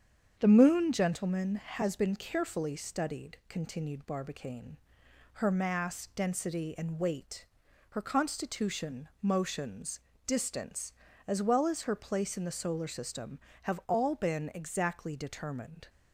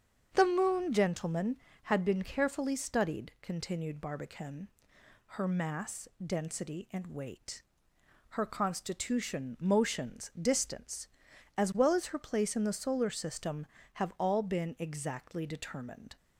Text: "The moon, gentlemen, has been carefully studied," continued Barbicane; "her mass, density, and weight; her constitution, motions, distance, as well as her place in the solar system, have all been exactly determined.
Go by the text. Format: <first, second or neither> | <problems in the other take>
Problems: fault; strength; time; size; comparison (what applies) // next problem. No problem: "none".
first | starts louder than the rest; strong; until 1.3 s; 7.5 dB; strong in the first // says "had" for "has"; at 1.8 s